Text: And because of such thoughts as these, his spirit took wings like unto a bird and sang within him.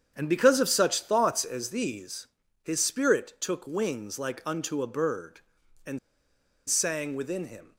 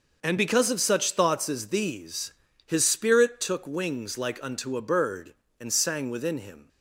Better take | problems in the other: second | starts louder than the rest; strong; until 1.1 s; 8 dB; noticeable in the second // pauses between "and" and "sang"; noticeable; at 5.9 s; 0.70 s long

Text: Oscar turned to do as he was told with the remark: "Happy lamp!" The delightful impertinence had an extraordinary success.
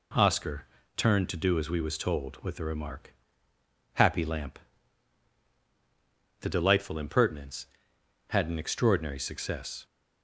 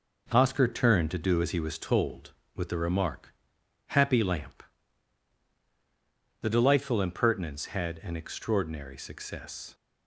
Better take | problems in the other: second | pauses between "Oscar" and "turned"; slight; at 0.6 s; 0.32 s long // says "we" for "he"; at 1.7 s

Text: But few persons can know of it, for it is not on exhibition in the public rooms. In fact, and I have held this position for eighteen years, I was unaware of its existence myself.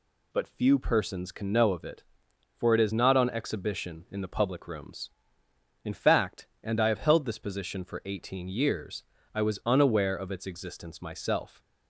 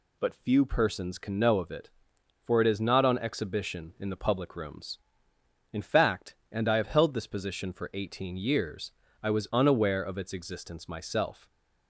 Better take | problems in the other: neither | none

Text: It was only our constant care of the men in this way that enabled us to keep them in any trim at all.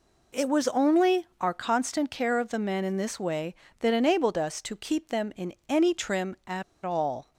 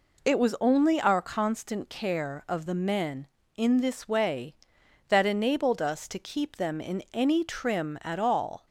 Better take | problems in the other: second | pauses between "in" and "any"; slight; at 5.5 s; 0.16 s long // pauses between "at" and "all"; slight; at 6.6 s; 0.22 s long

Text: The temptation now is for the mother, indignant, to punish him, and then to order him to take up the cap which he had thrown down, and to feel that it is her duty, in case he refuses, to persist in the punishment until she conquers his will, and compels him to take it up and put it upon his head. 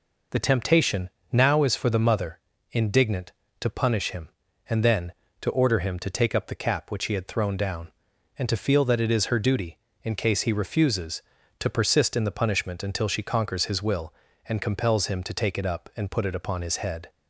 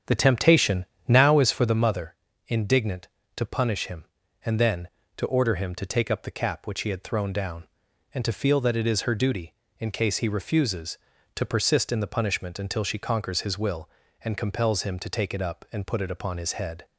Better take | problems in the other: first | starts louder than the rest; strong; until 1.8 s; 8.5 dB // pauses between "temptation" and "now"; slight; at 0.8 s; 0.24 s long; slight in the first

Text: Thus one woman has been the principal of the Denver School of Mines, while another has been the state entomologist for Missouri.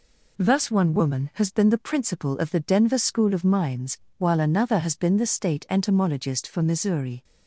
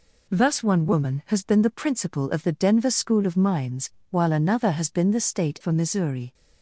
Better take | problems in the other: first | skips "entomologist"; at 5.5 s

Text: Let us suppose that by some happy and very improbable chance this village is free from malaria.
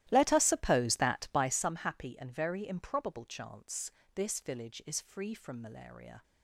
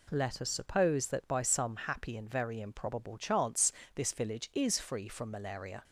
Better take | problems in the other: second | starts louder than the rest; strong; until 1.6 s; 14.5 dB // pauses between "chance" and "this"; slight; at 3.9 s; 0.24 s long; slight in the second

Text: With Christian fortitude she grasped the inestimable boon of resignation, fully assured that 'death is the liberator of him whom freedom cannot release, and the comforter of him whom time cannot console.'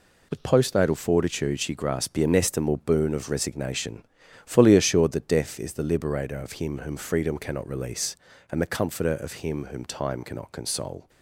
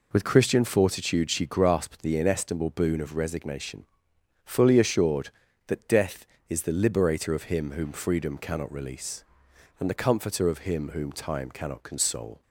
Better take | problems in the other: second | says "Postnatal" for "Christian"; at 0.4 s

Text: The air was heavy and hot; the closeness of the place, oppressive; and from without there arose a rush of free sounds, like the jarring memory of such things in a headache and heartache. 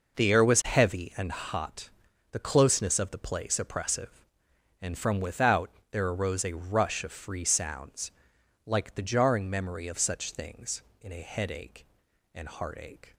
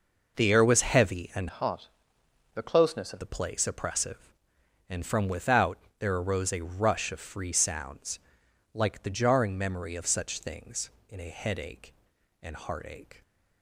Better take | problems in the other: first | changes voice from "hot" to "of"; from 1.4 to 3.1 s; 1.7 s long // pauses between "without" and "there"; slight; at 5.7 s; 0.22 s long; slight in the first

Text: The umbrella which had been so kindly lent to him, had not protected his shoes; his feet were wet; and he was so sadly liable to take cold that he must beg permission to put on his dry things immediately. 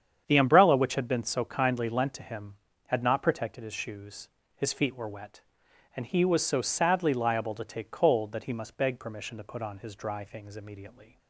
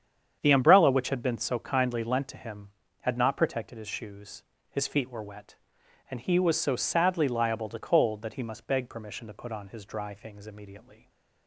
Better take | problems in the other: first | starts louder than the rest; strong; until 1.4 s; 8 dB; strong in the first // skips "take"; at 7.7 s // stays silent after the last word; slight; from 10.9 s on; 0.5 s long

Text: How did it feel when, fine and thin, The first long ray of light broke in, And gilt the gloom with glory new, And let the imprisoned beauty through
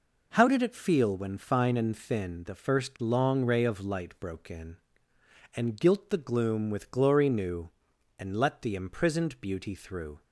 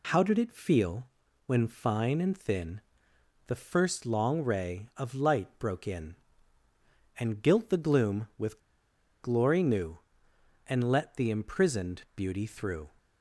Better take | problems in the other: first | pauses between "feel" and "when"; at 1.0 s; 0.40 s long // pauses between "with" and "glory"; noticeable; at 8.5 s; 0.62 s long

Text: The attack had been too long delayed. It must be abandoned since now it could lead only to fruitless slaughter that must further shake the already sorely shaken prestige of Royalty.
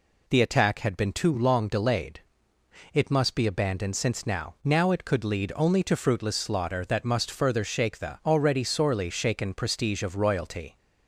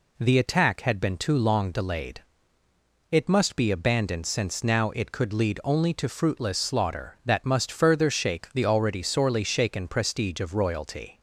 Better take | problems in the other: second | says "now" twice; at 4.6 s

